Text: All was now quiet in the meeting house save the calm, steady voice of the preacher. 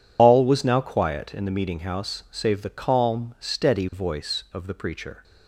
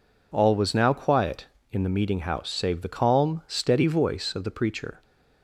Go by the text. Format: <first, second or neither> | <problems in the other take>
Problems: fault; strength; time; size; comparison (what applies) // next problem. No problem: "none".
second | loses the start of "All"; at 0.1 s; 75 ms